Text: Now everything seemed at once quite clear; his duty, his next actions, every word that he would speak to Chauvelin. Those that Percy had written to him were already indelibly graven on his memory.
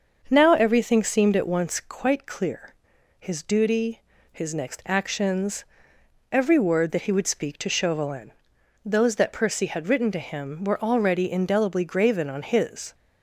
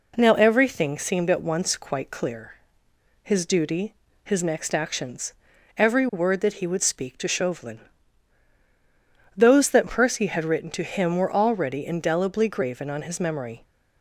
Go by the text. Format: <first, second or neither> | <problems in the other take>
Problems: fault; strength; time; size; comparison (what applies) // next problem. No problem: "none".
second | starts louder than the rest; until 1.2 s; 6.5 dB // stops before "memory"; at 12.9 s